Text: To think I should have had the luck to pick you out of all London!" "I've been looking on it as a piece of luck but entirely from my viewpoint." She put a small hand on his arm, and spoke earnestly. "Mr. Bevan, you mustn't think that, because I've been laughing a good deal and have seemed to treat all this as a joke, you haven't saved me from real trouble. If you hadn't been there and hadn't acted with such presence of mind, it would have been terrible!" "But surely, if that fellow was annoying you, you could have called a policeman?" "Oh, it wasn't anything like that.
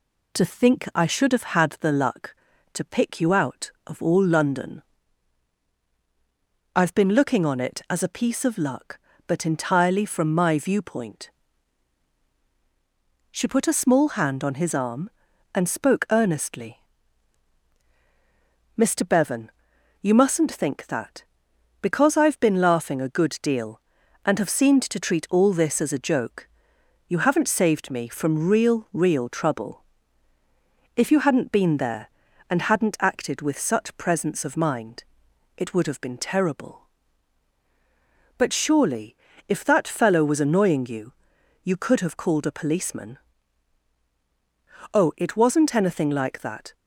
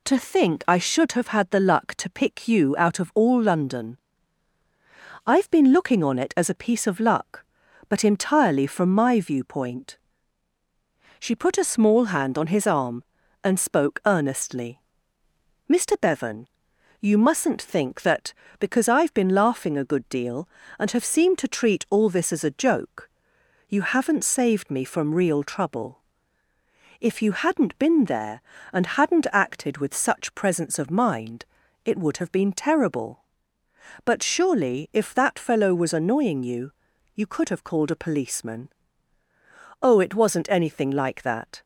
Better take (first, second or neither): second